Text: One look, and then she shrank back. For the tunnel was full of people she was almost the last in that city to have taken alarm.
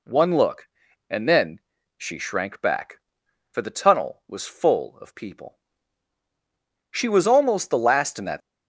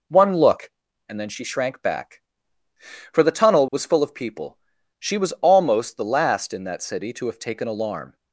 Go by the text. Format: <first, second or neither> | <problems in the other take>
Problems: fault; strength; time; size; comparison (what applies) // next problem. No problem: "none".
second | pauses between "then" and "she"; slight; at 1.6 s; 0.36 s long // pauses between "people" and "she"; strong; at 5.5 s; 1.3 s long; also in the second // stops before "city to have taken alarm"; at 8.4 s